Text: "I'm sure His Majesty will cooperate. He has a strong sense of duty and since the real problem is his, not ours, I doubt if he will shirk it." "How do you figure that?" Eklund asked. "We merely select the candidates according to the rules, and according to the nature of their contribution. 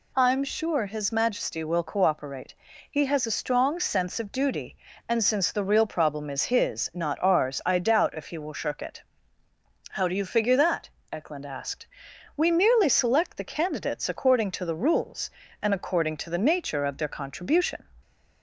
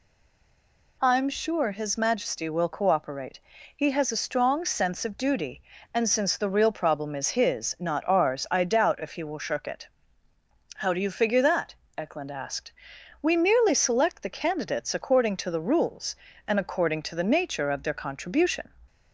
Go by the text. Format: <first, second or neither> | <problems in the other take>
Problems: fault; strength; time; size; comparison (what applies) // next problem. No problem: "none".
first | stays silent before the first word; until 1.0 s; 1.0 s long